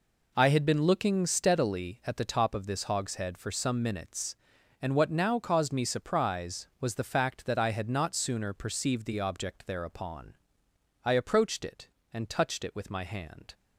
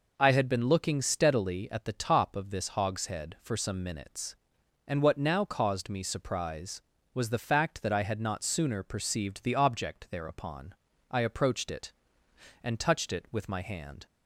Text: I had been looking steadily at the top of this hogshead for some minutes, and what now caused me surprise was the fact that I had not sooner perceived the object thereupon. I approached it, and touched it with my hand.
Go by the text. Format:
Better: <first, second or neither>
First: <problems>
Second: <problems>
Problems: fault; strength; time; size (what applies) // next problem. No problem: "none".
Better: neither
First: none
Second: none